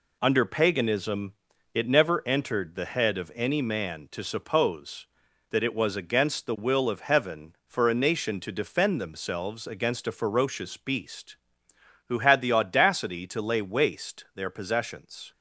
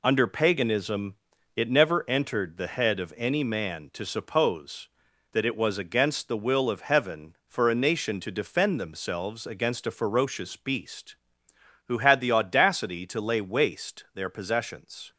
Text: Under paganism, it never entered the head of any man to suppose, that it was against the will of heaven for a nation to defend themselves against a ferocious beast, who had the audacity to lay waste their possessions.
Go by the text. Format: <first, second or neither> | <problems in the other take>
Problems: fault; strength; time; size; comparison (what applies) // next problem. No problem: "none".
neither | none